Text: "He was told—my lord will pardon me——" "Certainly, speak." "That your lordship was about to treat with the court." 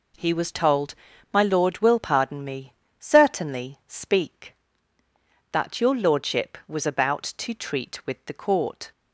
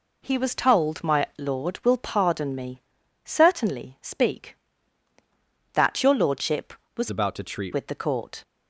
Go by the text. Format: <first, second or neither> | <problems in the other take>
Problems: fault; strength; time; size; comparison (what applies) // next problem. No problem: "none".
first | changes voice from "about" to "treat"; from 7.0 to 7.7 s; 0.7 s long